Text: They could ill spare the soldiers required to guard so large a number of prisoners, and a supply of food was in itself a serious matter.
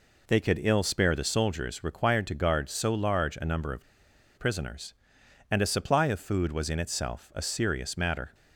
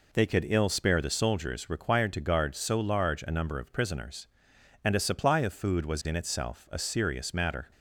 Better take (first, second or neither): second